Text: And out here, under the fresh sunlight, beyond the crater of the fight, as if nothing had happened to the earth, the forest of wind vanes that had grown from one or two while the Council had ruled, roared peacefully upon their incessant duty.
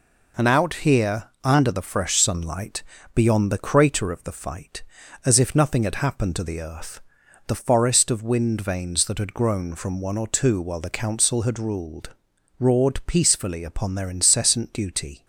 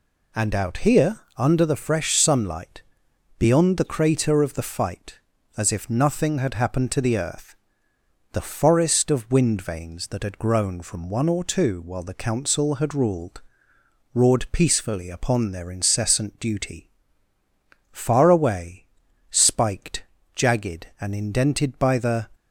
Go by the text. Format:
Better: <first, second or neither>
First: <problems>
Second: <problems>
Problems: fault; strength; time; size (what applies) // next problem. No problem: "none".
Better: first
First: none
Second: goes on to say "Far away spiked jagged and indented by the"; strong; from 17.9 s on; 4.3 s long